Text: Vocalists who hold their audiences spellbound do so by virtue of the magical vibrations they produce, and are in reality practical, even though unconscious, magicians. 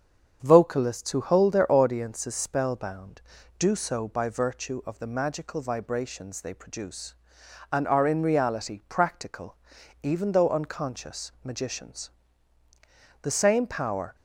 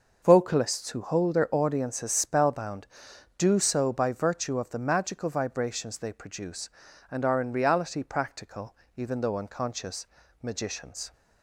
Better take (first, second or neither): second